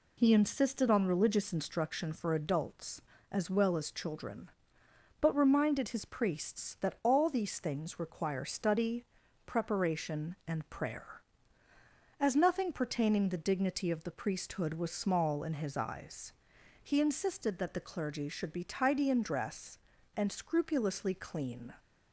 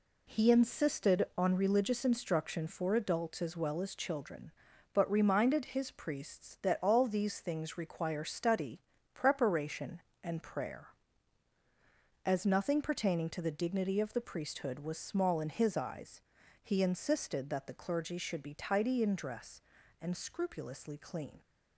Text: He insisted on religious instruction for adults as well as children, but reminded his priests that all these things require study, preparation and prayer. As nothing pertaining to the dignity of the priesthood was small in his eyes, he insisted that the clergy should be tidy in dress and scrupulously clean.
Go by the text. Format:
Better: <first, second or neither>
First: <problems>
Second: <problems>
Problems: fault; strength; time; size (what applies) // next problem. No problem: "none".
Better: second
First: skips "to"; at 13.2 s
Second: none